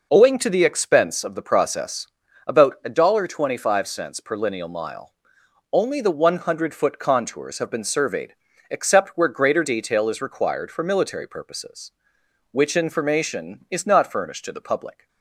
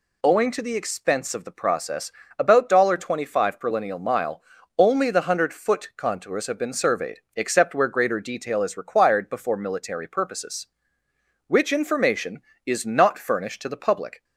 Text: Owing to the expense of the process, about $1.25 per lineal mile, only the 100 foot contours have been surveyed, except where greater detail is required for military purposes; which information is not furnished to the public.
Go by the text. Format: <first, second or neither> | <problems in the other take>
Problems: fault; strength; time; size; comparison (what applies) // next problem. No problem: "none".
first | says "before" for "for"; at 9.2 s